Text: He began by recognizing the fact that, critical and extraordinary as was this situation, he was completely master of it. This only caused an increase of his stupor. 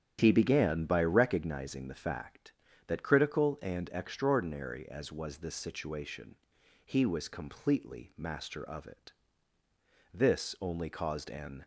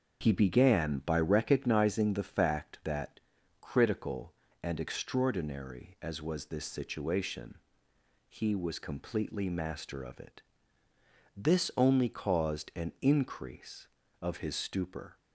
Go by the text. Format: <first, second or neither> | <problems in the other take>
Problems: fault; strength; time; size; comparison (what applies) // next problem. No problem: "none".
second | starts louder than the rest; strong; until 1.2 s; 9.5 dB; also in the second // stops before "increase of his stupor"; at 11.6 s